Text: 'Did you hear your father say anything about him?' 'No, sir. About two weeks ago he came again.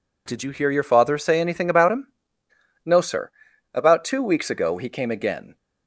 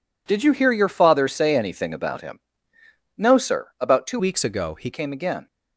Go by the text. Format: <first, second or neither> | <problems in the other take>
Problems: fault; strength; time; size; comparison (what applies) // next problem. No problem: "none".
first | changes voice from "weeks" to "he"; from 4.1 to 4.8 s; 0.7 s long